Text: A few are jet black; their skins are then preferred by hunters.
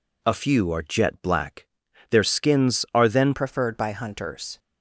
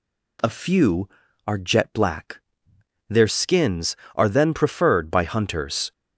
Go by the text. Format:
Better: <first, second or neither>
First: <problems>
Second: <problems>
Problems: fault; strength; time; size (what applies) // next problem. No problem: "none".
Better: second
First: changes voice at "preferred"; from 3.3 s on; 1.2 s long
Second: none